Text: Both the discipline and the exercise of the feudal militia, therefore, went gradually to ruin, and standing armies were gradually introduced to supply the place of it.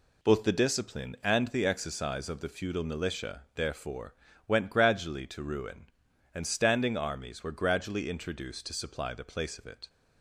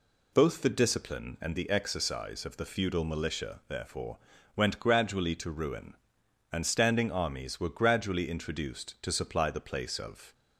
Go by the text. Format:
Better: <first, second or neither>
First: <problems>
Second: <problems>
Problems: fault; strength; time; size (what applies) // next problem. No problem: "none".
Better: first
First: none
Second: stops before "it"; at 10.3 s